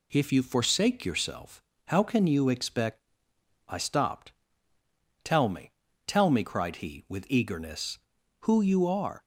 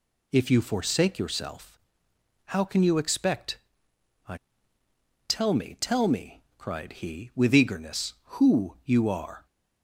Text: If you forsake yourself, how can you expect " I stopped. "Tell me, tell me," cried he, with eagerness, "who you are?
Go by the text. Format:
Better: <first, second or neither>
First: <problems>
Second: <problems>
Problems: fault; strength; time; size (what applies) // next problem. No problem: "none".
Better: first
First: none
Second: skips "stopped"; at 4.8 s